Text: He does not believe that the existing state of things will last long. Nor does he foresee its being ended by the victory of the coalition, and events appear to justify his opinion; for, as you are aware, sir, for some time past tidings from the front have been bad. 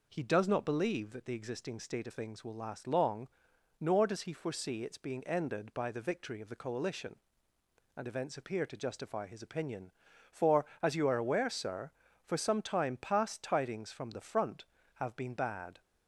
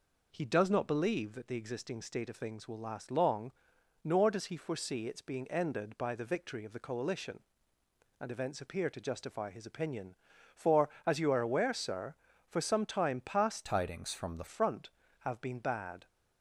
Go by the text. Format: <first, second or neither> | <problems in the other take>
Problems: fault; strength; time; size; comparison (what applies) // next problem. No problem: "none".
first | changes voice from "tidings" to "the"; from 13.6 to 14.4 s; 0.8 s long